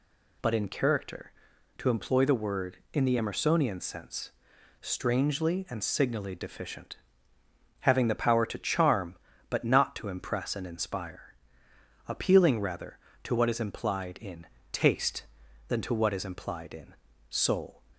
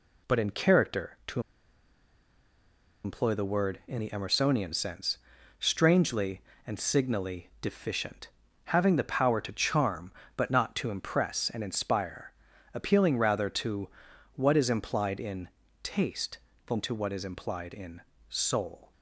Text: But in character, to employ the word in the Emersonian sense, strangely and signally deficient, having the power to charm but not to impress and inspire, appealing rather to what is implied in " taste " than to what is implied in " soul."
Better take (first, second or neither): first